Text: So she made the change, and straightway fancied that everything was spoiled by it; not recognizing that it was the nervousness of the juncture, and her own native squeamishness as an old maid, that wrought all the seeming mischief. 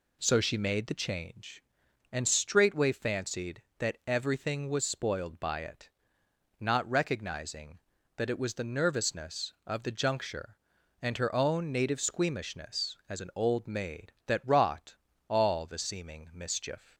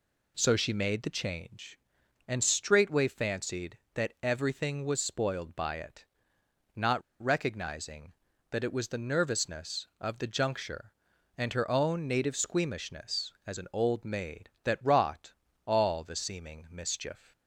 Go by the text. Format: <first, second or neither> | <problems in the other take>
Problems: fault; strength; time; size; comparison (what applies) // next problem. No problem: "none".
first | pauses between "not" and "recognizing"; slight; at 7.0 s; 0.22 s long // pauses between "wrought" and "all"; slight; at 15.3 s; 0.34 s long; slight in the first